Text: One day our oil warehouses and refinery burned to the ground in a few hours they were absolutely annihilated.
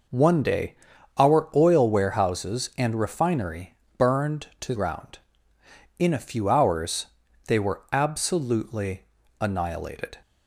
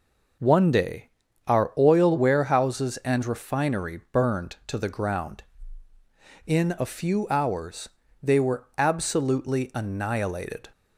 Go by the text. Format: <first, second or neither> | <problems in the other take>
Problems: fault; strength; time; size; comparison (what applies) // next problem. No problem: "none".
second | pauses between "day" and "our"; at 0.7 s; 0.44 s long; also in the second // pauses between "refinery" and "burned"; slight; at 3.7 s; 0.24 s long // skips "the"; at 4.7 s // pauses between "hours" and "they"; at 7.0 s; 0.40 s long; slight in the second // pauses between "absolutely" and "annihilated"; slight; at 9.0 s; 0.36 s long